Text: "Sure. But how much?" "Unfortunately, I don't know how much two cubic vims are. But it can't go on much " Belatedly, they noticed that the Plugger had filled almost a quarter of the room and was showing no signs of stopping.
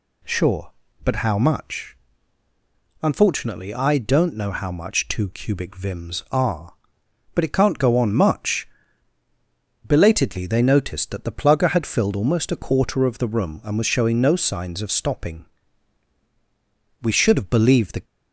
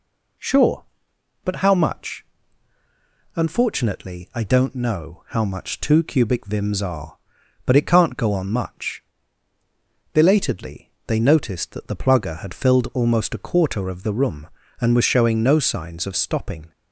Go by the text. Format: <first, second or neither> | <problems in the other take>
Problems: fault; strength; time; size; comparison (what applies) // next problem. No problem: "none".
second | goes on to say "We should have believed the"; noticeable; from 17.0 s on; 1.0 s long